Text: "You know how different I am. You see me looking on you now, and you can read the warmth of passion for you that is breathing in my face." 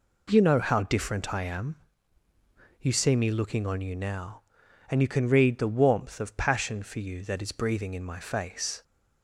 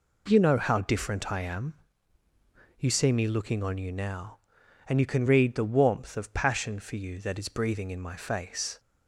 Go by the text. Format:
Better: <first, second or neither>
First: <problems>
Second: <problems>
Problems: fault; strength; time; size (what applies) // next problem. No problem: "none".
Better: neither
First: none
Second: none